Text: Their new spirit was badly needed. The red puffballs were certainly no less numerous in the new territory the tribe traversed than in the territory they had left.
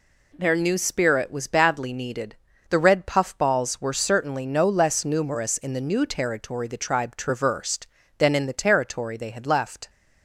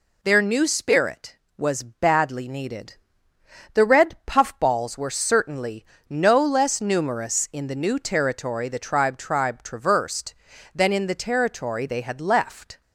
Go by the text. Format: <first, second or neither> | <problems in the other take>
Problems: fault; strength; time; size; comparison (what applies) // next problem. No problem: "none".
first | pauses between "certainly" and "no"; slight; at 5.8 s; 0.24 s long // says "tribe" twice; at 9.1 s